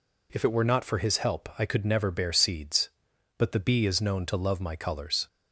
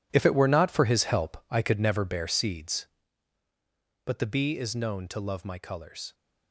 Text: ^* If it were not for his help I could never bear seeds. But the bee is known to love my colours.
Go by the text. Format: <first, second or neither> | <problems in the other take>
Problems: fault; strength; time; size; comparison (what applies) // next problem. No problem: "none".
first | gets quieter; strong; throughout; 13.5 dB